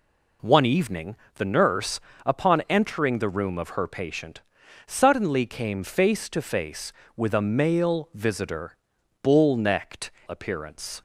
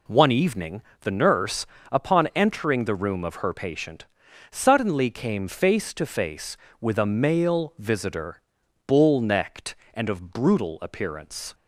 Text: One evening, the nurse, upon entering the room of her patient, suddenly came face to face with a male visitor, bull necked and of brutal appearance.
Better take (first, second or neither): second